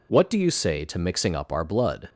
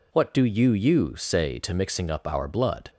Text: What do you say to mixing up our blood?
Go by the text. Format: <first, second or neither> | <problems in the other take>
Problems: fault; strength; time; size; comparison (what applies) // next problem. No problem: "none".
first | says "you" twice; at 0.7 s